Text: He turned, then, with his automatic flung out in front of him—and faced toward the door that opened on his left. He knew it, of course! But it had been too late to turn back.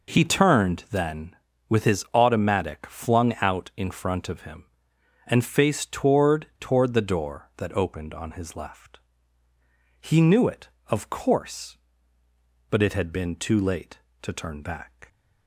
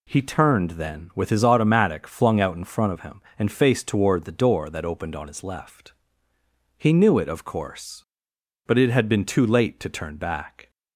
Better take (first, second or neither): second